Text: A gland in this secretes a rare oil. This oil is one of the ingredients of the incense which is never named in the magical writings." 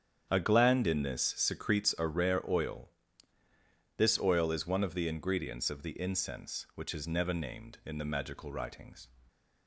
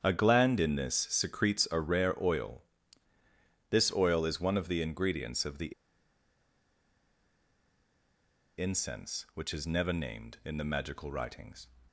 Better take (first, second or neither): first